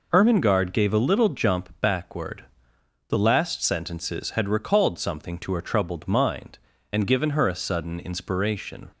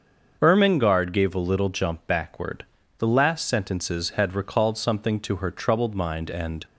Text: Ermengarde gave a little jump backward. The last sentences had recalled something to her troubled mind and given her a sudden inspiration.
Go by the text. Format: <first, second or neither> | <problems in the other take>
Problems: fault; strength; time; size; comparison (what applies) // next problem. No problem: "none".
first | starts louder than the rest; until 1.4 s; 6.5 dB // stops before "given her a sudden inspiration"; at 6.6 s